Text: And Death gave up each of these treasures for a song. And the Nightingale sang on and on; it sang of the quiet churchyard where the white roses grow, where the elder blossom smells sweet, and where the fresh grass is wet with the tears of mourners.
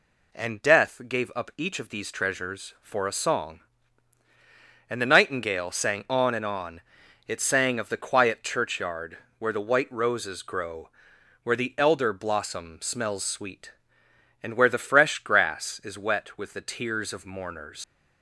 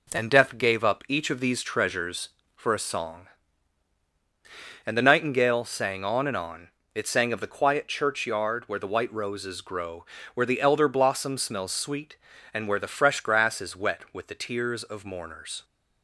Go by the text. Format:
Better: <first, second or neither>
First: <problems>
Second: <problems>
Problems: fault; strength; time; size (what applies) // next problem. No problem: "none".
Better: second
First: pauses between "churchyard" and "where"; slight; at 9.1 s; 0.22 s long // leaves "mourners" unfinished; at 17.8 s; 110 ms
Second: none